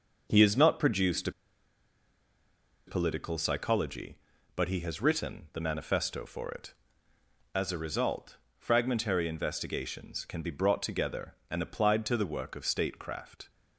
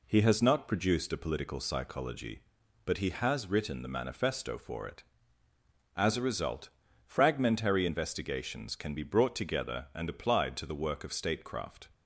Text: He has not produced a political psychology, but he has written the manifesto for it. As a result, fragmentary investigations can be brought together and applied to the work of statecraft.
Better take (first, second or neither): second